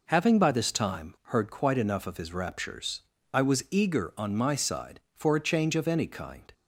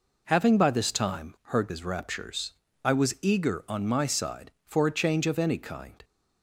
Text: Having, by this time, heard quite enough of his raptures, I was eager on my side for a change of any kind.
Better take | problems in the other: first | skips "quite enough of"; at 1.6 s

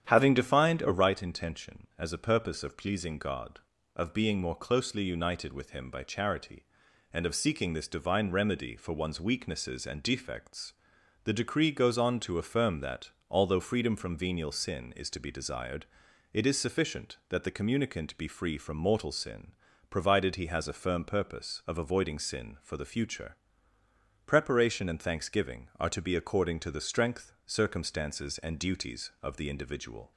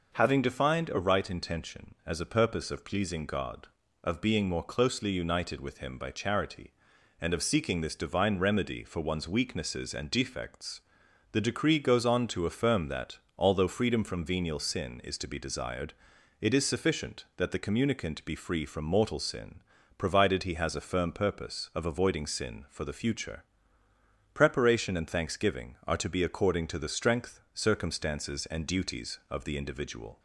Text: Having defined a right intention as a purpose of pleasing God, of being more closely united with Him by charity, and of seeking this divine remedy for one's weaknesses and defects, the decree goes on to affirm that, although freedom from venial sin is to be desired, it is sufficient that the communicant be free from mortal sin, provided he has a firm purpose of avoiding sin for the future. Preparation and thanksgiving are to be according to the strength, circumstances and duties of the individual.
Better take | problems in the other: second | starts louder than the rest; strong; until 1.2 s; 9.5 dB

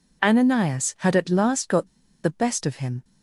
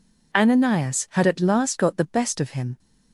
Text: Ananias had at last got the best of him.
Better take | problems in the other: second | pauses between "got" and "the"; slight; at 1.8 s; 0.35 s long

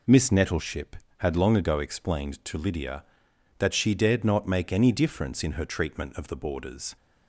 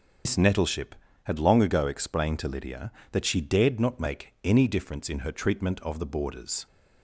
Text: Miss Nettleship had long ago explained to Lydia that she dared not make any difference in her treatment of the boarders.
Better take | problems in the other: first | loses the start of "Miss"; at 0.2 s; 110 ms // starts louder than the rest; until 1.5 s; 6.5 dB

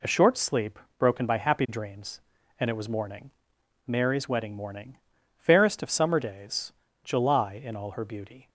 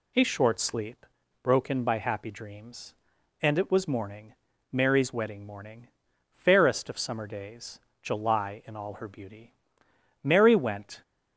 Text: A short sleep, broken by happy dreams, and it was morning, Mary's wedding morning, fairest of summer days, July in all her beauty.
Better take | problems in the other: first | goes on to say "Mary went"; noticeable; from 10.2 s on; 0.78 s long

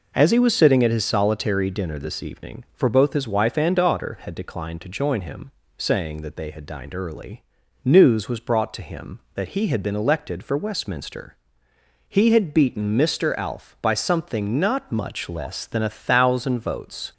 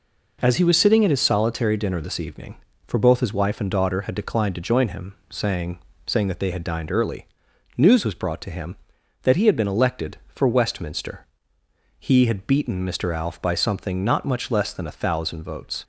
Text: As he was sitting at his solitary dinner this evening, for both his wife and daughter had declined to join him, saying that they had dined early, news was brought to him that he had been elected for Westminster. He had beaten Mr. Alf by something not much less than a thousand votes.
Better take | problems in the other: first | says "saying" twice; at 6.0 s

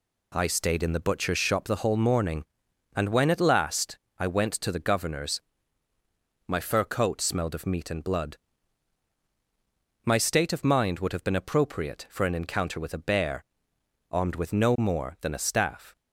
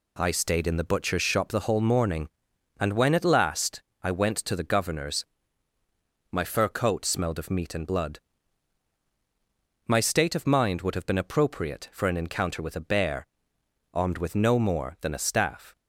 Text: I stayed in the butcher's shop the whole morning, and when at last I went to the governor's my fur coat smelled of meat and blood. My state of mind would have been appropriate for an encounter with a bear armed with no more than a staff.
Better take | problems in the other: neither | pauses between "last" and "I"; slight; the same in both // pauses between "governor's" and "my"; the same in both // pauses between "bear" and "armed"; noticeable; the same in both

